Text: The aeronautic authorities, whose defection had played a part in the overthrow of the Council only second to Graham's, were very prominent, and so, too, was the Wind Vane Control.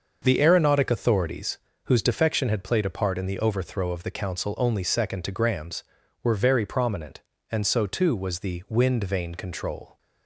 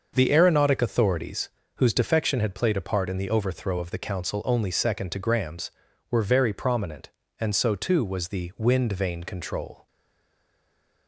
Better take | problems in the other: first | starts louder than the rest; until 1.1 s; 6.5 dB; also in the first // stays silent after the last word; noticeable; from 9.8 s on; 1.2 s long

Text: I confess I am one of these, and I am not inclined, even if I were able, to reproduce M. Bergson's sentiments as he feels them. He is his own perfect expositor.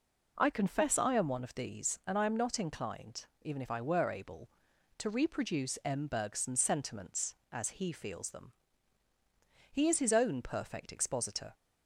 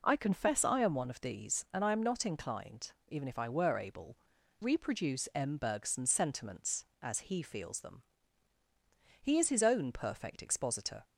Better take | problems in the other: first | skips "to"; at 4.3 s

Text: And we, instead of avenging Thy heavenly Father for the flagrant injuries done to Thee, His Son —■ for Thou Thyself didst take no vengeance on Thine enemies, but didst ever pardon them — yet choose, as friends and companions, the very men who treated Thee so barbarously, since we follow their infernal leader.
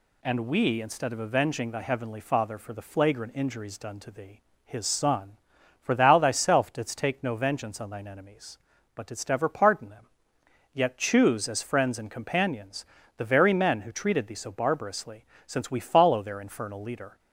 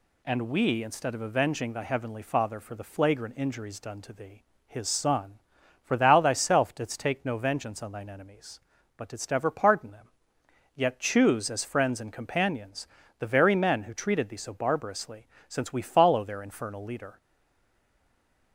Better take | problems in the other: first | stays silent after the last word; noticeable; from 17.2 s on; 1.3 s long

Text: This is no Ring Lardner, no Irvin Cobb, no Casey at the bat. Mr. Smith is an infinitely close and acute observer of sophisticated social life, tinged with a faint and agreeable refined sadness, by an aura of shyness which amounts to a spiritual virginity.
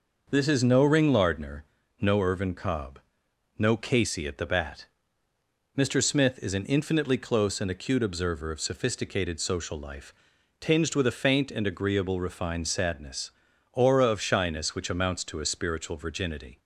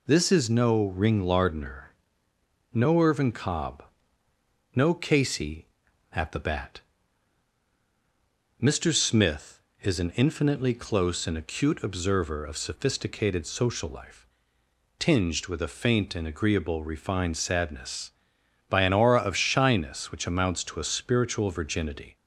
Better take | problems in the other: second | starts louder than the rest; noticeable; until 1.3 s; 6 dB // skips "by an"; at 13.5 s

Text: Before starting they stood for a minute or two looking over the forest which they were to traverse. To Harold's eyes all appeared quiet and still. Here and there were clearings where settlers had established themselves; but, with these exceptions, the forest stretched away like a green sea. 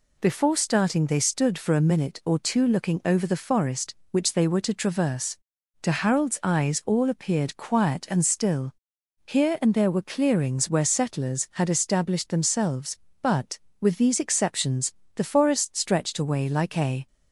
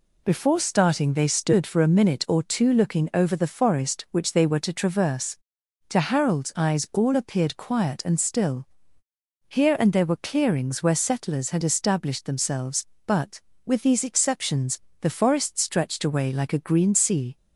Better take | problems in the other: second | stops before "green sea"; at 17.0 s

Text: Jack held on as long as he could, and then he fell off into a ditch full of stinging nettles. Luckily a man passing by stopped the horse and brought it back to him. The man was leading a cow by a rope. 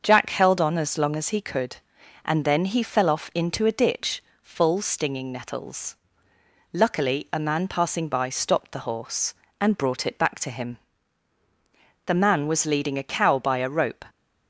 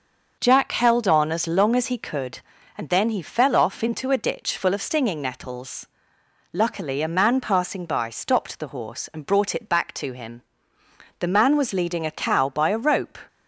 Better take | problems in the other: second | starts louder than the rest; until 1.0 s; 6.5 dB // pauses between "ditch" and "full"; slight; at 4.2 s; 0.20 s long // skips "of"; at 4.8 s

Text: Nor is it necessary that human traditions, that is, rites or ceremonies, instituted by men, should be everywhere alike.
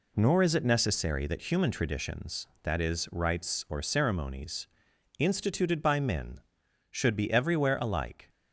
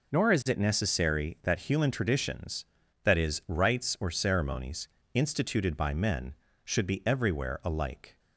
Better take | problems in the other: neither | none

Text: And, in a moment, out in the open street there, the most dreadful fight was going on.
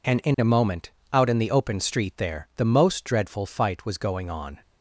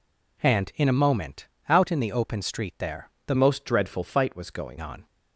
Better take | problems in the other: first | changes voice from "most" to "going"; from 3.3 to 4.7 s; 1.4 s long

